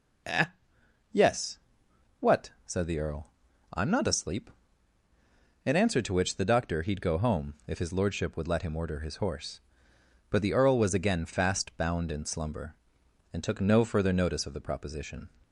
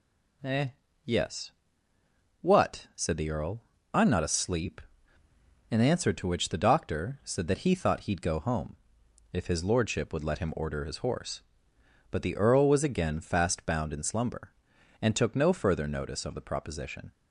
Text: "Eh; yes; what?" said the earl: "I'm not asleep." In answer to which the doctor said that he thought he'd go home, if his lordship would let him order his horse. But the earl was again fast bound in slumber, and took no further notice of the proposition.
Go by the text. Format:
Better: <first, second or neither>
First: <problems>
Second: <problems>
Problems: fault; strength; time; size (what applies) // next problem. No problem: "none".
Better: second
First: skips "said that he thought"; at 6.8 s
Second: none